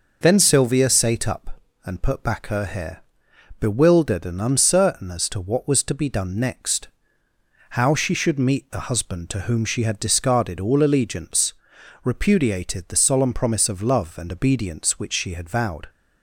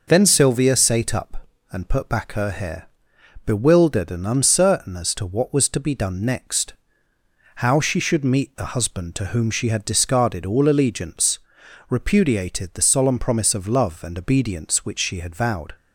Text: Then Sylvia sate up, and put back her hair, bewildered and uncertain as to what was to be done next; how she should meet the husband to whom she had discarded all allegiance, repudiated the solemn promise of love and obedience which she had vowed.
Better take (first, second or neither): neither